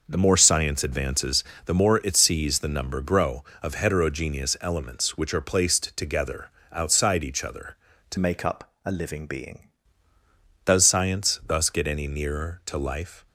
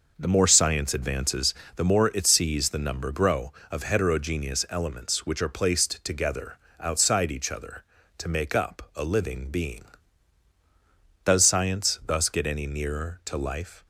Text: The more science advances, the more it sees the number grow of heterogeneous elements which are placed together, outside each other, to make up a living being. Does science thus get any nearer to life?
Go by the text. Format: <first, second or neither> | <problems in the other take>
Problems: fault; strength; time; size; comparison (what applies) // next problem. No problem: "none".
second | changes voice from "make" to "being"; from 8.1 to 9.6 s; 1.5 s long